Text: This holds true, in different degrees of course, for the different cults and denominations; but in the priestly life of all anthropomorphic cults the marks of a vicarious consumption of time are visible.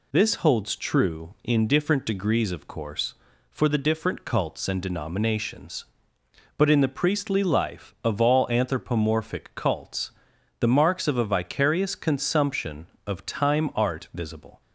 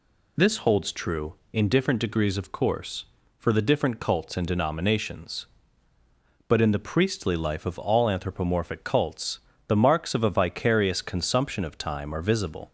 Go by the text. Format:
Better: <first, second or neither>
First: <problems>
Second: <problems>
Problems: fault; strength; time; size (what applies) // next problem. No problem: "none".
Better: second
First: pauses between "cults" and "the"; noticeable; at 10.1 s; 0.48 s long // says "art" for "are"; at 13.7 s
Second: pauses between "cults" and "the"; slight; at 9.3 s; 0.28 s long